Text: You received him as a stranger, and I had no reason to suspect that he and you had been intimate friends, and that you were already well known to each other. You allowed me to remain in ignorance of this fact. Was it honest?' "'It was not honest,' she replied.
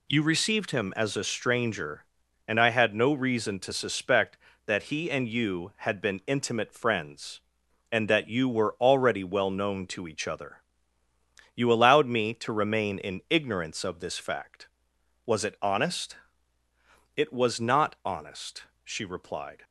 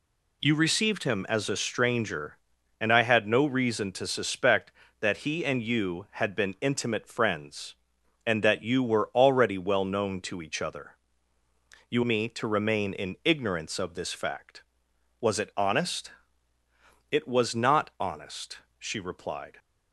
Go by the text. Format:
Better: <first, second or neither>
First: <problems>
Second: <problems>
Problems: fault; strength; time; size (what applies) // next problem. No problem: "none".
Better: first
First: none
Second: skips "allowed"; at 12.0 s